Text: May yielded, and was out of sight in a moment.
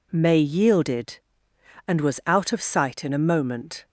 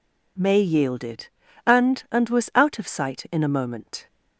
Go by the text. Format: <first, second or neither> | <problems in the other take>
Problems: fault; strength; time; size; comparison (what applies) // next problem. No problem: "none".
first | says "and" twice; at 2.1 s